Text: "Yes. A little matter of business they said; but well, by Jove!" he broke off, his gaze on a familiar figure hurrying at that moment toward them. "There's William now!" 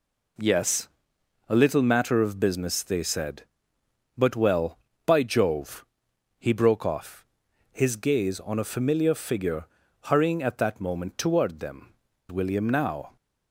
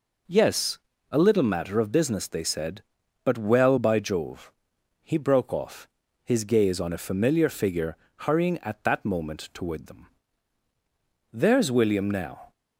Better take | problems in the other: second | pauses between "figure" and "hurrying"; at 9.6 s; 0.38 s long; slight in the second // skips "There's"; at 12.1 s

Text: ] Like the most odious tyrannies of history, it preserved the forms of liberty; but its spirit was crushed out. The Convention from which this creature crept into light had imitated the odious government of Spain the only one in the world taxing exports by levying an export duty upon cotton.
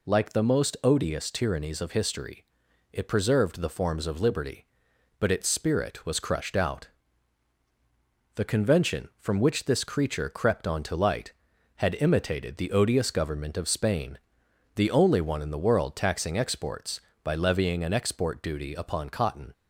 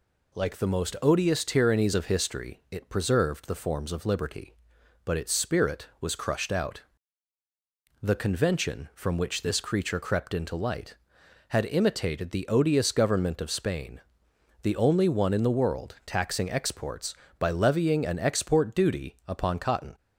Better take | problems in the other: second | says "onto" for "into"; at 10.6 s // pauses between "Spain" and "the"; noticeable; at 14.1 s; 0.56 s long; noticeable in the second

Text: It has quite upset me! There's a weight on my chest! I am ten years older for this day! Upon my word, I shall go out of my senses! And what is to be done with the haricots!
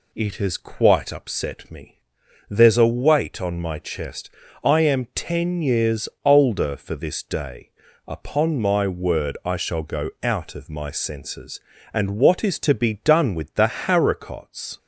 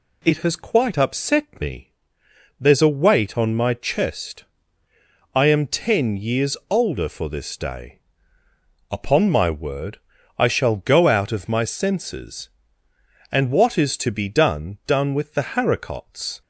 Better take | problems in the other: first | pauses between "years" and "older"; slight; at 6.5 s; 0.16 s long; slight in the first // says "done" twice; at 14.8 s

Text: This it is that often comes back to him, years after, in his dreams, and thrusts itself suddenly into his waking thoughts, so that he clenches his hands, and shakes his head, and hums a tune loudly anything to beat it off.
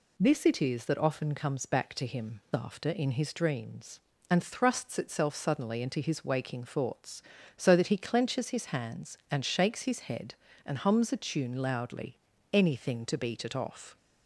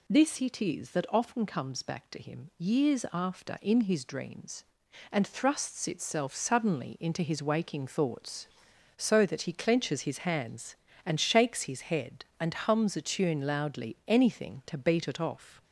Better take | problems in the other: second | skips "years"; at 2.4 s // pauses between "loudly" and "anything"; at 12.1 s; 0.38 s long

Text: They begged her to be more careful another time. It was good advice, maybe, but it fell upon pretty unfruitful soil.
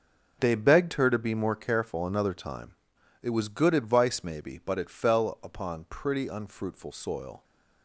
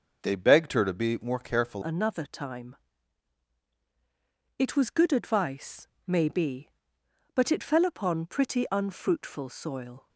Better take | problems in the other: first | changes voice at "another"; from 1.8 s on; 8.2 s long

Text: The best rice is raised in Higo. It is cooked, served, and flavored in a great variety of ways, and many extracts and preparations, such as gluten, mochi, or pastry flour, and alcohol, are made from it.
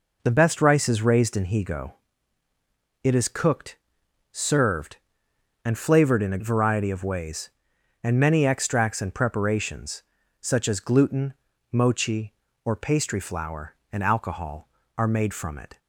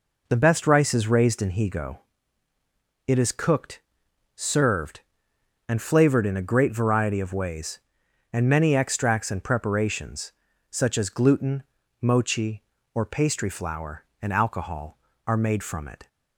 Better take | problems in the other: second | skips "great"; at 6.3 s

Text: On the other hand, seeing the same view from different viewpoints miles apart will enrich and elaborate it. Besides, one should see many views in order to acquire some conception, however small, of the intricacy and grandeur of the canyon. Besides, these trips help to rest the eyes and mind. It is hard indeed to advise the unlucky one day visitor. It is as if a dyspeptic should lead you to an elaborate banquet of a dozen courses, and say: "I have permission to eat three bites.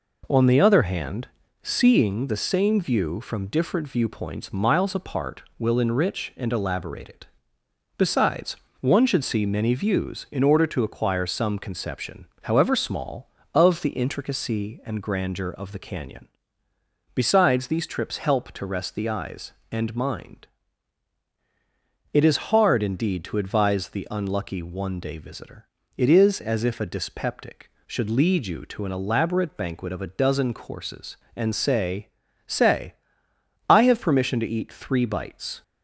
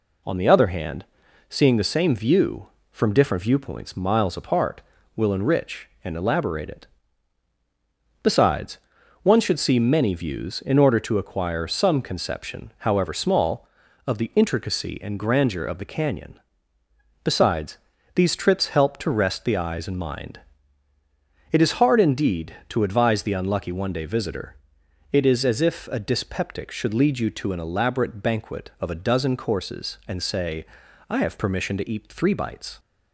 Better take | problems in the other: second | says "say" twice; at 32.4 s

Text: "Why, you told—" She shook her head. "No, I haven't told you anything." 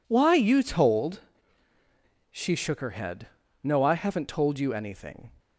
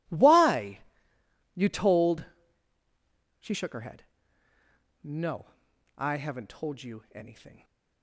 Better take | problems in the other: neither | none

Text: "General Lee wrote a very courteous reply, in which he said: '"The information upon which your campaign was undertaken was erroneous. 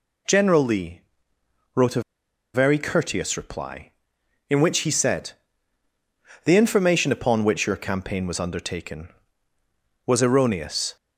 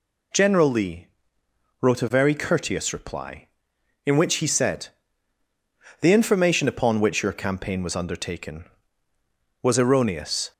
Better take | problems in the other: second | pauses between "Lee" and "wrote"; noticeable; at 1.0 s; 0.74 s long; noticeable in the second // pauses between "a" and "very"; noticeable; at 2.0 s; 0.53 s long

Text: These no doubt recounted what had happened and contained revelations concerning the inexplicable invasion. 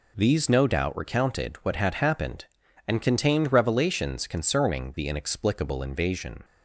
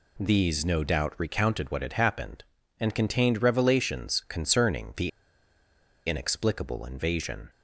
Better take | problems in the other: first | pauses between "the" and "inexplicable"; noticeable; at 5.0 s; 0.97 s long

